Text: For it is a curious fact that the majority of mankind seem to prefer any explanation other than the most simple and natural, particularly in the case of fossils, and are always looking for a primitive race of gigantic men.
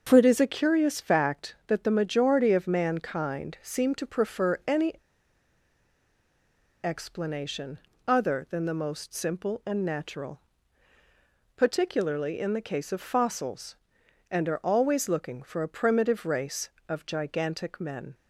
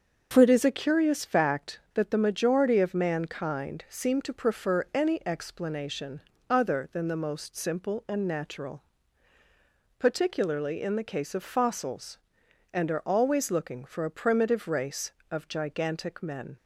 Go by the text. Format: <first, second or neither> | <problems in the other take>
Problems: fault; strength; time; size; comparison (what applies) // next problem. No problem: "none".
second | starts louder than the rest; until 1.0 s; 6.5 dB; also in the second // pauses between "any" and "explanation"; strong; at 4.9 s; 1.8 s long // pauses between "explanation" and "other"; slight; at 7.8 s; 0.28 s long; slight in the second